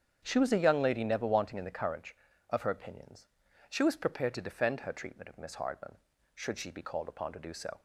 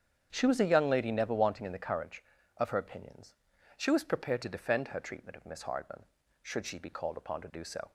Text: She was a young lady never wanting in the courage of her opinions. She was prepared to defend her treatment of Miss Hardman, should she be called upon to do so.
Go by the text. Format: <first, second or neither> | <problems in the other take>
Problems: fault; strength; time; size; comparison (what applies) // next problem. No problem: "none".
neither | starts louder than the rest; strong; the same in both